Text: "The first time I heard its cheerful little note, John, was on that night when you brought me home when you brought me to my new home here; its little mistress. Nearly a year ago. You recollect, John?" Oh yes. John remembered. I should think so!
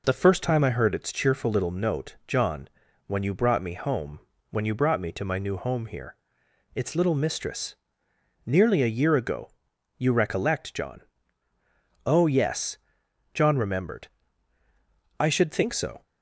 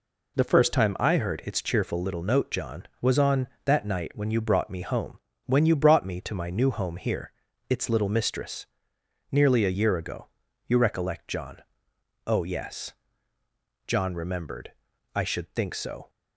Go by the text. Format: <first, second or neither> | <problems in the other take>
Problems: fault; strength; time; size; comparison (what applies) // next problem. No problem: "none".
second | skips "was on that night"; at 2.8 s // pauses between "home" and "when"; slight; at 4.1 s; 0.32 s long; slight in the second